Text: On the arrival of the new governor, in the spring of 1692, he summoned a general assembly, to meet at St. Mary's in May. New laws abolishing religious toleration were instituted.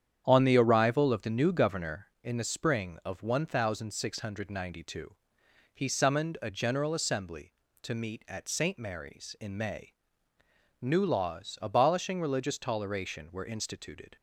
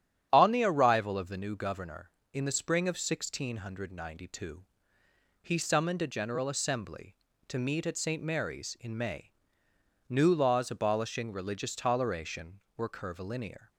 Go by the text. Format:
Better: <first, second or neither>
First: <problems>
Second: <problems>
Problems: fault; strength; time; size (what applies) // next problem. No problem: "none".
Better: first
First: starts louder than the rest; strong; until 1.2 s; 9 dB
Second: starts louder than the rest; strong; until 1.3 s; 10.5 dB // says "curvilinear" for "instituted"; at 12.8 s